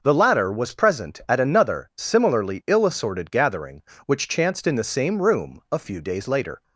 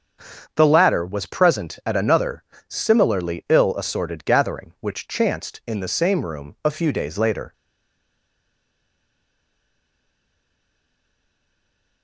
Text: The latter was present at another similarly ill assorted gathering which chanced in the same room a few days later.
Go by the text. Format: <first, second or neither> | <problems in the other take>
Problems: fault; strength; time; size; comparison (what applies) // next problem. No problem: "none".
first | starts louder than the rest; until 1.5 s; 7 dB // pauses between "another" and "similarly"; slight; at 2.4 s; 0.26 s long // stays silent after the last word; strong; from 7.5 s on; 4.5 s long